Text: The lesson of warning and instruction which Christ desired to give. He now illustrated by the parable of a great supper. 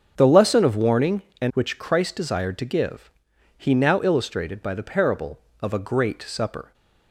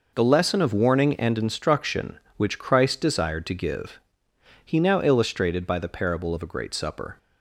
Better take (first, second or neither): second